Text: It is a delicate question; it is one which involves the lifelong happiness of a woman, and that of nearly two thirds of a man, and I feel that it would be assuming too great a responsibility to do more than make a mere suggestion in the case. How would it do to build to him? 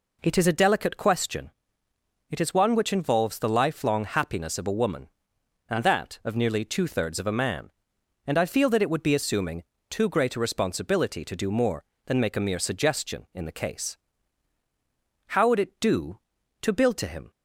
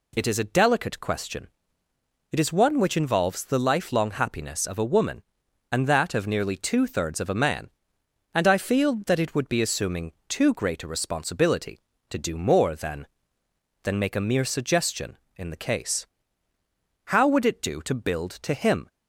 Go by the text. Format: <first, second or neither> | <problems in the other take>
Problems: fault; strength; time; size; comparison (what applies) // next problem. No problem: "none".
first | pauses between "assuming" and "too"; slight; at 10.1 s; 0.16 s long; slight in the first // says "than" twice; at 13.8 s